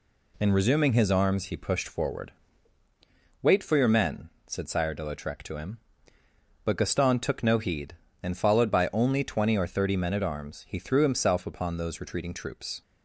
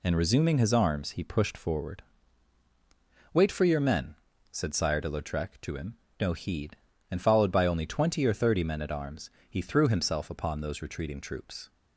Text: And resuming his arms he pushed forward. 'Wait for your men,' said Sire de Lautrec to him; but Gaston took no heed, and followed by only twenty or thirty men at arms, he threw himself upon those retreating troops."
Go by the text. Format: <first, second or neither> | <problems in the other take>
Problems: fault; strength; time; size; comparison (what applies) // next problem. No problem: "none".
first | skips "but Gaston took"; at 6.0 s